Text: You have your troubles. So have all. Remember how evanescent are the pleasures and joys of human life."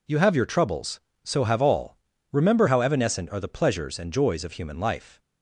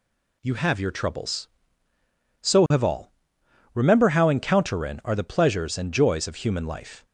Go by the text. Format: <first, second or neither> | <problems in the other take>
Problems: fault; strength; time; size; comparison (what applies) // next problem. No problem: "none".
first | says "encounterin" for "evanescent"; at 4.2 s